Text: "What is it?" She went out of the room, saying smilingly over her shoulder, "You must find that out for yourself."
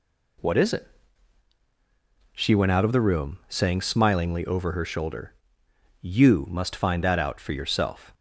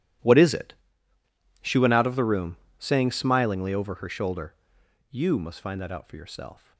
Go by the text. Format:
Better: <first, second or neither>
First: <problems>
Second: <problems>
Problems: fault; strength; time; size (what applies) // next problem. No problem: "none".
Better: first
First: none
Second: gets quieter; strong; throughout; 18 dB